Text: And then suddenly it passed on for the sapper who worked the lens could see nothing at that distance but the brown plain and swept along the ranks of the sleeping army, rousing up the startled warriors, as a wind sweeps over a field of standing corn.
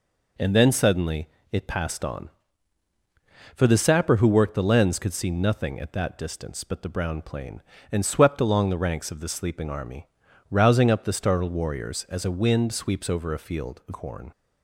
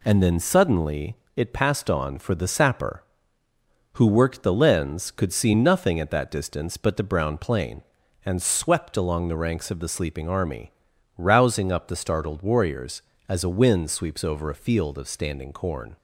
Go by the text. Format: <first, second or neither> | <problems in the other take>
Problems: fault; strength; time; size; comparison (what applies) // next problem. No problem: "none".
second | pauses between "suddenly" and "it"; slight; at 1.2 s; 0.24 s long; slight in the second // skips "standing"; at 13.9 s